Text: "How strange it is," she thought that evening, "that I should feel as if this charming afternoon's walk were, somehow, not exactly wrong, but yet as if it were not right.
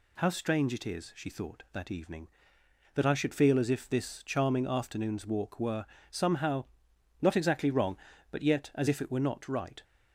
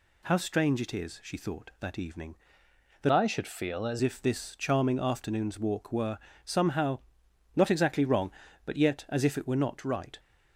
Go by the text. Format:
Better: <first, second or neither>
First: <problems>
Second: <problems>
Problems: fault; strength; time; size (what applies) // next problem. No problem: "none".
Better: first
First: none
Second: changes voice from "I" to "as"; from 3.1 to 3.9 s; 0.8 s long